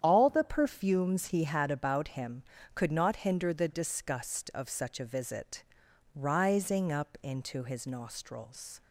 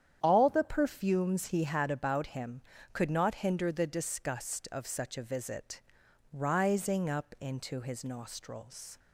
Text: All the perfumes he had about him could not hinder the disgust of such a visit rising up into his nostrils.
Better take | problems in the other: neither | starts louder than the rest; strong; the same in both // pauses between "visit" and "rising"; noticeable; the same in both

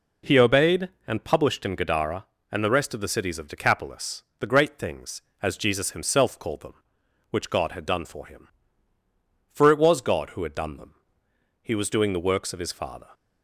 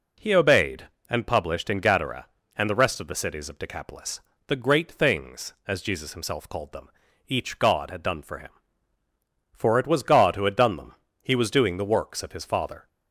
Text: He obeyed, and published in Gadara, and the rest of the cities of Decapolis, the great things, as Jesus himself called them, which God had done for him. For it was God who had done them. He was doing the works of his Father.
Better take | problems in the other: first | says "each" for "which"; at 7.2 s

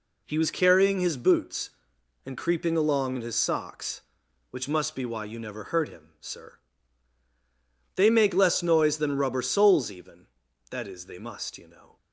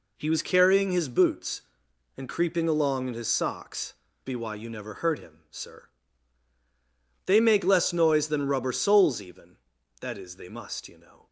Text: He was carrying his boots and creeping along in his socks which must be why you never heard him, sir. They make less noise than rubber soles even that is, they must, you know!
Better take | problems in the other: first | skips "which must"; at 4.0 s

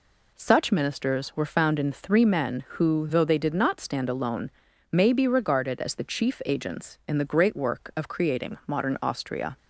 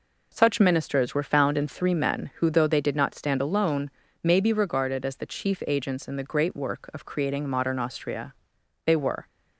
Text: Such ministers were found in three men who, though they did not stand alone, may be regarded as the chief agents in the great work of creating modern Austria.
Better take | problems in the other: first | goes on to say "They were"; slight; from 8.8 s on; 0.40 s long

